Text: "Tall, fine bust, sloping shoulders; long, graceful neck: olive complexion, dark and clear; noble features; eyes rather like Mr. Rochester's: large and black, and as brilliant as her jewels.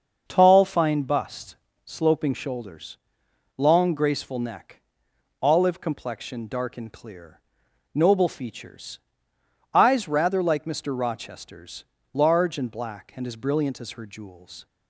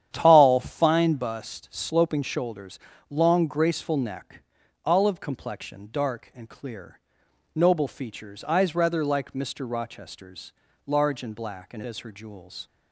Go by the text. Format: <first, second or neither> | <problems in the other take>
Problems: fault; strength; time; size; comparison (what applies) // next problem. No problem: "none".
first | starts louder than the rest; strong; until 1.1 s; 9.5 dB; also in the first // skips "as brilliant"; at 11.8 s